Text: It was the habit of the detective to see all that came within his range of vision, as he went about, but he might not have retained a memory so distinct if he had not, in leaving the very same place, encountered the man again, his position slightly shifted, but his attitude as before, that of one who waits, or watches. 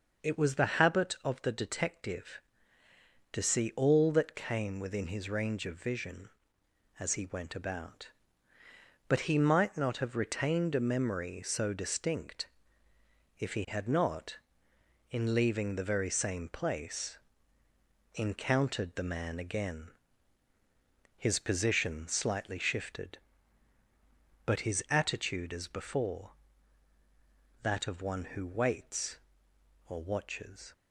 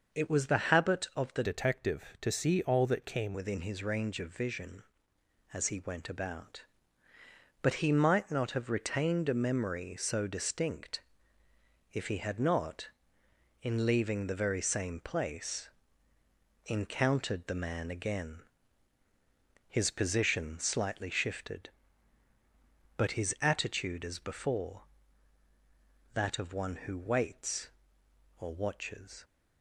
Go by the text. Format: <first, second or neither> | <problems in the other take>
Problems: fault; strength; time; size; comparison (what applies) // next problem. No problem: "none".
first | starts louder than the rest; until 1.2 s; 6 dB; also in the first // changes voice from "detective" to "came"; from 1.4 to 3.3 s; 1.9 s long // pauses between "distinct" and "if"; noticeable; at 11.0 s; 0.90 s long; noticeable in the first